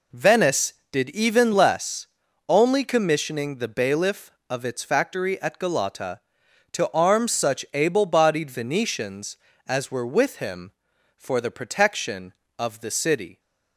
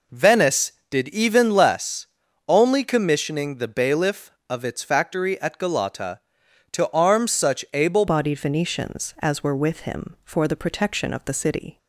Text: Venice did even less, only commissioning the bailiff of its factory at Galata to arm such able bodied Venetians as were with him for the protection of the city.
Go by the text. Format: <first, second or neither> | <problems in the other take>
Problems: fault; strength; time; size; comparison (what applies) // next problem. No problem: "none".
first | changes voice at "bodied"; from 8.0 s on; 3.7 s long